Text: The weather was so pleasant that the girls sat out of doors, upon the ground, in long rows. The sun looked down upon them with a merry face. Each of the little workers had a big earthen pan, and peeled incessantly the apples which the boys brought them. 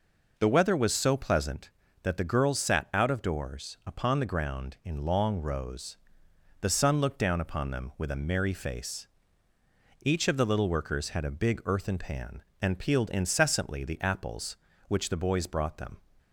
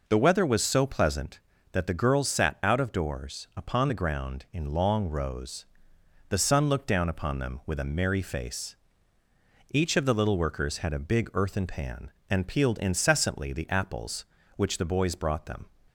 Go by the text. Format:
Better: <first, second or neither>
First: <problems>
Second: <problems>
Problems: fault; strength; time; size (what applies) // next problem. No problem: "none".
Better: neither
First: none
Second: none